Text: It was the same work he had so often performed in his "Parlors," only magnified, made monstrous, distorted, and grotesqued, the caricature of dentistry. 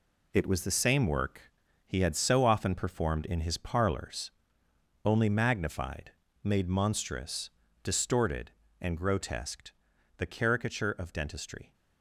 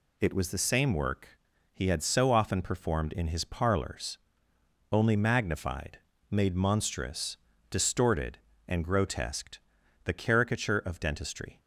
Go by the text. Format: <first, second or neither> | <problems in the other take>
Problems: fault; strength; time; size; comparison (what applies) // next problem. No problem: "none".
second | gets quieter; strong; throughout; 7.5 dB // pauses between "work" and "he"; slight; at 1.5 s; 0.36 s long; slight in the second